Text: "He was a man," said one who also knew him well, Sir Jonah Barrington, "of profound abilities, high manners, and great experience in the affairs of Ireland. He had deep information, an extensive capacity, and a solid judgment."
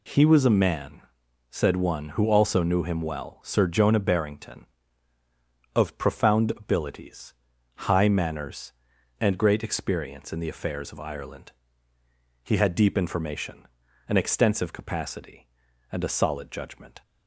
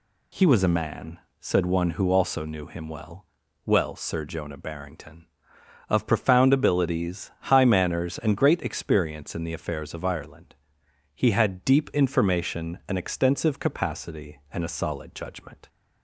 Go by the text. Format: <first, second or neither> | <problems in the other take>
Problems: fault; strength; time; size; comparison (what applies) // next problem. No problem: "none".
first | says "well" twice; at 3.6 s